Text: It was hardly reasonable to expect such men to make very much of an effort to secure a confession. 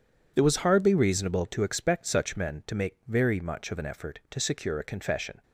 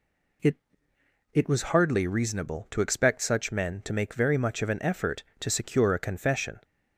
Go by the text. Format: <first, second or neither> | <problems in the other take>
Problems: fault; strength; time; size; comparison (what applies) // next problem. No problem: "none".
first | says "It" twice; at 1.3 s